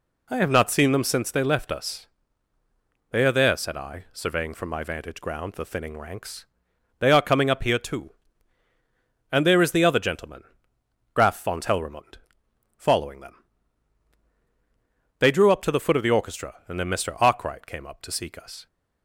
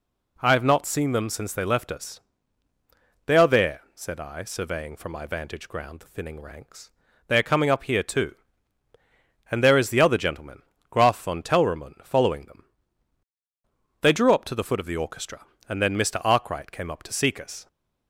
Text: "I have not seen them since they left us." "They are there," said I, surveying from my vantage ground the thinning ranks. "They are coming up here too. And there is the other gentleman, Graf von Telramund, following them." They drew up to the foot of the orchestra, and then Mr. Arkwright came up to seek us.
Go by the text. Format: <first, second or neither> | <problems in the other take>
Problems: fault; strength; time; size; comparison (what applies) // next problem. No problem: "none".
neither | none